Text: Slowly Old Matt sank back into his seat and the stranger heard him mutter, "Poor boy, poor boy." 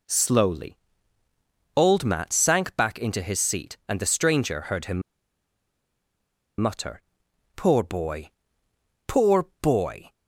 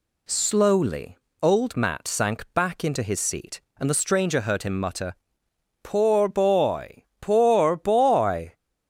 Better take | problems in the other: second | pauses between "Slowly" and "Old"; at 0.7 s; 1.0 s long; slight in the second // pauses between "him" and "mutter"; strong; at 5.0 s; 1.5 s long

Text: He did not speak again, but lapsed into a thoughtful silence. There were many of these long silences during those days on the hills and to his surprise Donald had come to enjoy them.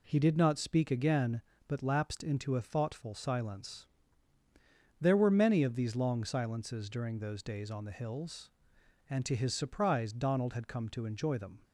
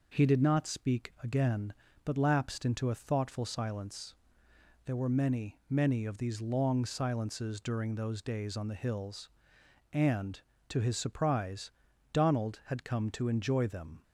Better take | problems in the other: first | says "many" twice; at 5.7 s // pauses between "surprise" and "Donald"; at 11.7 s; 0.42 s long

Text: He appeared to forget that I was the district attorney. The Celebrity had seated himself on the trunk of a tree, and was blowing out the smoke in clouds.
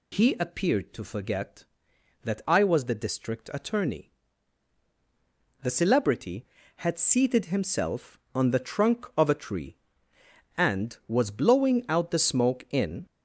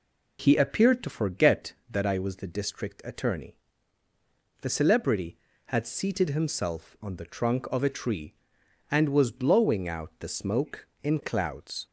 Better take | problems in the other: second | stops before "clouds"; at 13.0 s

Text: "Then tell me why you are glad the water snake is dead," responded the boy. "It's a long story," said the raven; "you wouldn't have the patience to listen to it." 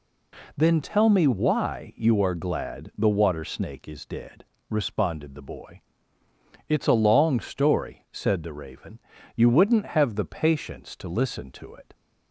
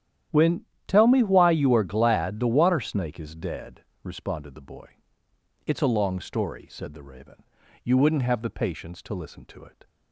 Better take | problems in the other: first | starts louder than the rest; strong; until 1.5 s; 11 dB // says "When" for "Then"; at 0.3 s

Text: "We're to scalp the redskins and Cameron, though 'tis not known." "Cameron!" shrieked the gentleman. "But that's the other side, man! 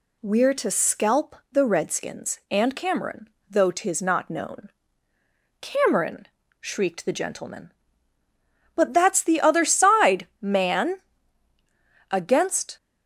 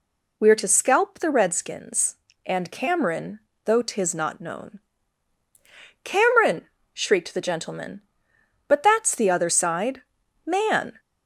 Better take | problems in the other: second | pauses between "scalp" and "the"; slight; at 1.3 s; 0.16 s long // goes on to say "Against"; noticeable; from 12.1 s on; 0.66 s long

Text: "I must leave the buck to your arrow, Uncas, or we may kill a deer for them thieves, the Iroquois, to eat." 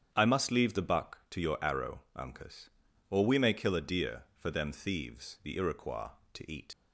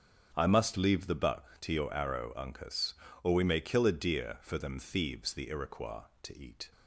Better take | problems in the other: second | starts louder than the rest; strong; until 1.1 s; 8.5 dB; also in the second // leaves "eat" unfinished; at 6.7 s; 90 ms

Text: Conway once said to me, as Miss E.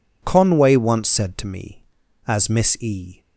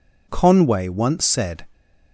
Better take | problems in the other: first | stops before "to me as Miss E"; at 1.7 s

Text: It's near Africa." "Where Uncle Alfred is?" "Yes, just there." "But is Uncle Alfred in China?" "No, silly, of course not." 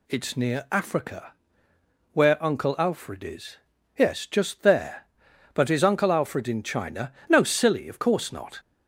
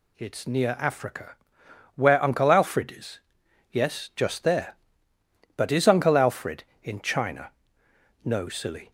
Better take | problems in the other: first | stops before "of course not"; at 8.8 s

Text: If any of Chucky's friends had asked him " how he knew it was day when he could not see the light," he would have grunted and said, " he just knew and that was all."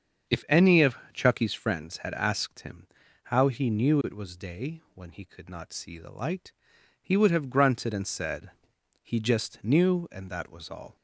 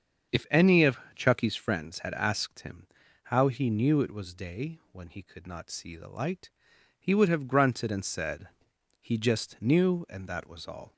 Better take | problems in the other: neither | starts louder than the rest; strong; the same in both // pauses between "of" and "Chucky's"; slight; the same in both

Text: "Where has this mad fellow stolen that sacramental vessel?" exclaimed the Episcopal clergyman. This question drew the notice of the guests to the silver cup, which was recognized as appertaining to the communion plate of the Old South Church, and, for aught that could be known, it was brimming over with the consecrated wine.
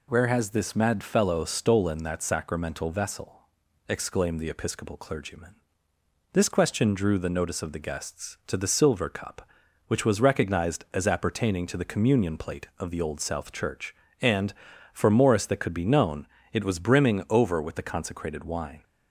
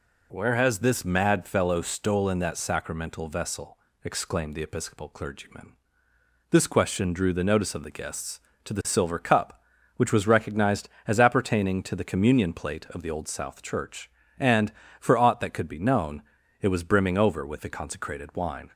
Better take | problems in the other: second | says "morris" for "aught"; at 15.1 s

